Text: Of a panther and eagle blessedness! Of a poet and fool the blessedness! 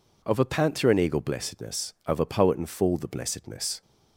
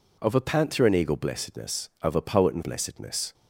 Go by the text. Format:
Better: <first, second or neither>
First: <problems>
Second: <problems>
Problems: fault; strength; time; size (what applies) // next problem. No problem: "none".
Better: first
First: none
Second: skips "fool the"; at 2.6 s